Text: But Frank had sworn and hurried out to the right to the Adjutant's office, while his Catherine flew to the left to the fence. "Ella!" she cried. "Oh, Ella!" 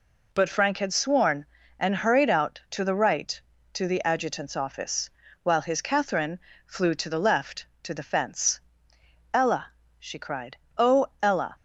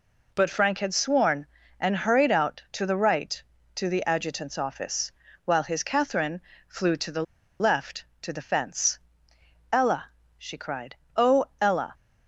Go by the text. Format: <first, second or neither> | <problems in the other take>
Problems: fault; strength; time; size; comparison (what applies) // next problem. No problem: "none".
first | pauses between "Catherine" and "flew"; slight; at 6.4 s; 0.28 s long; slight in the first // pauses between "the" and "left"; at 7.2 s; 0.37 s long